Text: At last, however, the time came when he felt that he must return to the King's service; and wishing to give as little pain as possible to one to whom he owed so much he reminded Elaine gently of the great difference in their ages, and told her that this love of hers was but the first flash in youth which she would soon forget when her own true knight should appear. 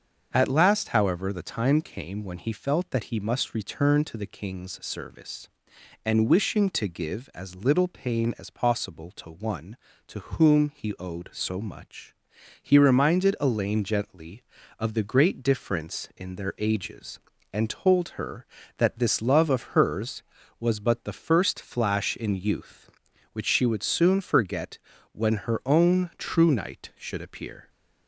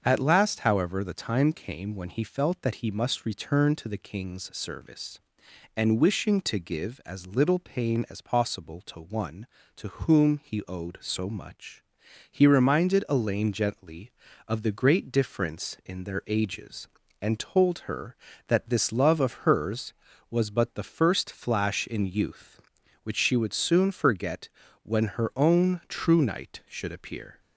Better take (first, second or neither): neither